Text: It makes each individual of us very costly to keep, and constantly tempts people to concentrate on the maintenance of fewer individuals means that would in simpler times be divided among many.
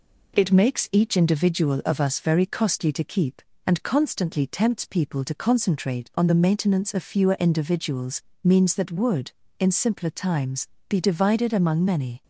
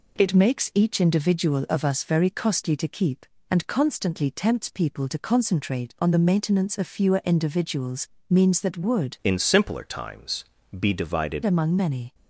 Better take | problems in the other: first | pauses between "individuals" and "means"; slight; at 8.0 s; 0.20 s long; slight in the first // changes voice from "in" to "divided"; from 9.2 to 11.4 s; 2.2 s long // pauses between "times" and "be"; slight; at 10.4 s; 0.34 s long; slight in the first

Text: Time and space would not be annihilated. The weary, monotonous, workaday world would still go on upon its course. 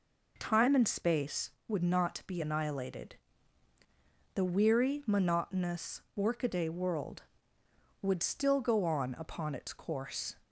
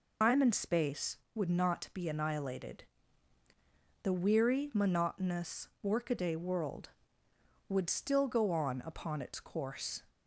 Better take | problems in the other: first | loses the start of "Time"; at 0.2 s; 185 ms

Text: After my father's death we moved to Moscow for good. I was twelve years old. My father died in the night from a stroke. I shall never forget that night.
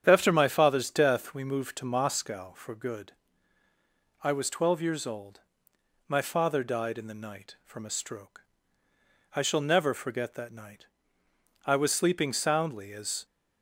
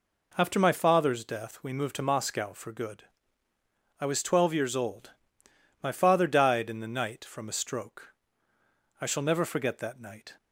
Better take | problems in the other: second | starts louder than the rest; strong; until 1.0 s; 9 dB // goes on to say "I was sleeping soundly as"; from 11.6 s on; 1.6 s long

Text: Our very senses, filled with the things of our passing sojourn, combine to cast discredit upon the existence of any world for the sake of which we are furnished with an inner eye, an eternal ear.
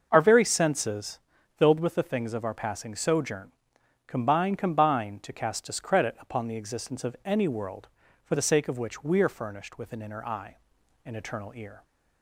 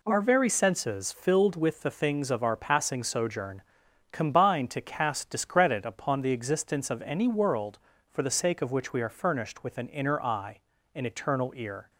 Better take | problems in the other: second | starts louder than the rest; noticeable; until 1.1 s; 6 dB // says "combine" twice; at 4.5 s

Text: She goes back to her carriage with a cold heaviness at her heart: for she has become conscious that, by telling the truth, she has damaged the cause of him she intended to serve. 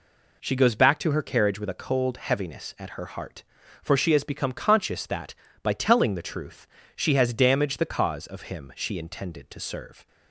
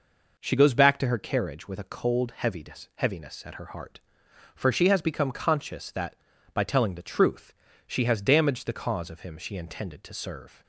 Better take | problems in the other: first | says "heaviness" twice; at 2.9 s

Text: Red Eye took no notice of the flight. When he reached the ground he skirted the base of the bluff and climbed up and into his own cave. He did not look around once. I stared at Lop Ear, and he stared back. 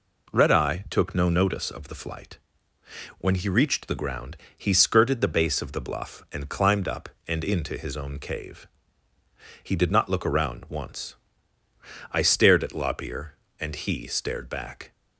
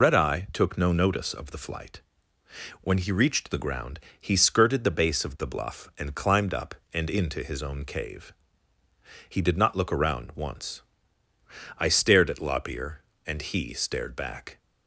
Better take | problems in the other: first | loses the start of "Red"; at 0.0 s; 100 ms // pauses between "ground" and "he"; slight; at 3.9 s; 0.22 s long; slight in the first

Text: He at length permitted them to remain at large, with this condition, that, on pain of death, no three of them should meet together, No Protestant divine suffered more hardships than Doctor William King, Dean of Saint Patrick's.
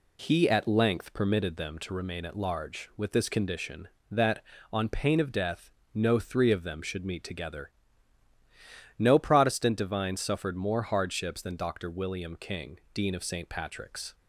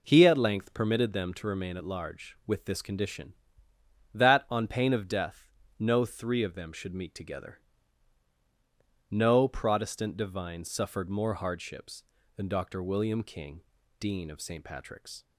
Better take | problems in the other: neither | none

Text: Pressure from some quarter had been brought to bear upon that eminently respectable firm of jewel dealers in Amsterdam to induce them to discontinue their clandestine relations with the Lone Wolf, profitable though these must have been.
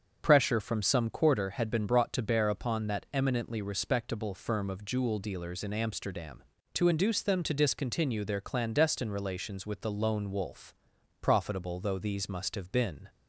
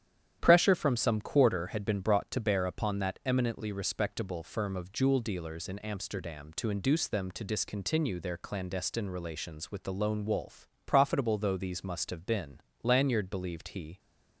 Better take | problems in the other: first | starts louder than the rest; strong; until 1.4 s; 10 dB; also in the first // goes on to say "Lanyard believed he"; noticeable; from 12.8 s on; 1.1 s long

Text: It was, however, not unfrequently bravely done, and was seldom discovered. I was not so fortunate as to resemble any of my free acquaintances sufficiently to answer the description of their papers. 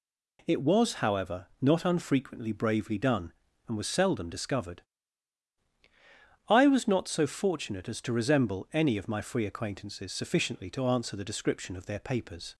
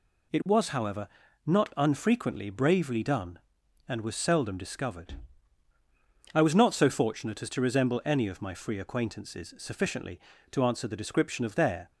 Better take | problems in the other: first | stops before "papers"; at 11.9 s

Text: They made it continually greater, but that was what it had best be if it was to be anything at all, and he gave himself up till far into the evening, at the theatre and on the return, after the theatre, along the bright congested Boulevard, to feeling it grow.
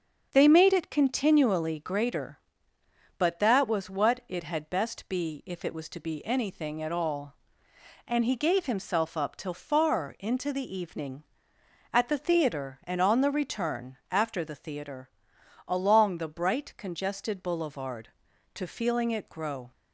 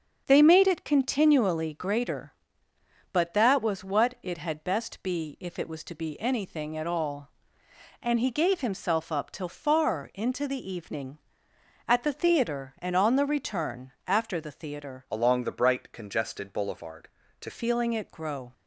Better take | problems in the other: first | starts louder than the rest; until 1.2 s; 6.5 dB; also in the first // changes voice from "along" to "to"; from 15.1 to 17.5 s; 2.4 s long

